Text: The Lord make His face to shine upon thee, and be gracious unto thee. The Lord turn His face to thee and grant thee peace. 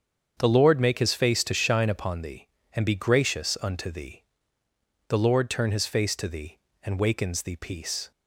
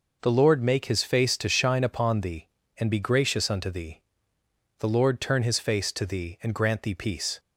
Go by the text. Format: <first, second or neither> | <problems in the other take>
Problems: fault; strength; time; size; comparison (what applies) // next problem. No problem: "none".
second | starts louder than the rest; strong; until 1.3 s; 7 dB // says "wakens" for "grant"; at 6.9 s